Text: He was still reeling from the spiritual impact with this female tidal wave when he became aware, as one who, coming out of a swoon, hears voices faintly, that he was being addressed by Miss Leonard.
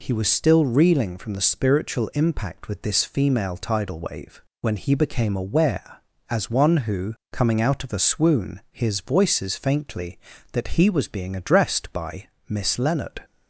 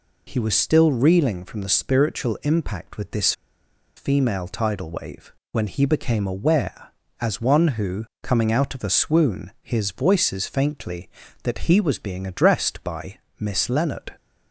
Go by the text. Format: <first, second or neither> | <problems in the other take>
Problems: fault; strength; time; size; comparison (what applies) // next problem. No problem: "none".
first | pauses between "this" and "female"; noticeable; at 3.3 s; 0.64 s long // pauses between "wave" and "when"; slight; at 5.3 s; 0.20 s long; slight in the first // pauses between "by" and "Miss"; slight; at 13.1 s; 0.18 s long; slight in the first